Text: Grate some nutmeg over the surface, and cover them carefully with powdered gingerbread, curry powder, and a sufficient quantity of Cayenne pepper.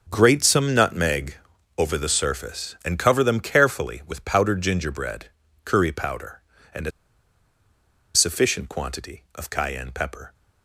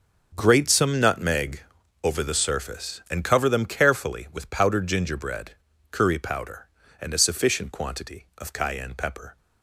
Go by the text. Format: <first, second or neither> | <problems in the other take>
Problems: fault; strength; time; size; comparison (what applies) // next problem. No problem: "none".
second | pauses between "nutmeg" and "over"; at 1.3 s; 0.44 s long; also in the second // pauses between "a" and "sufficient"; strong; at 6.9 s; 1.2 s long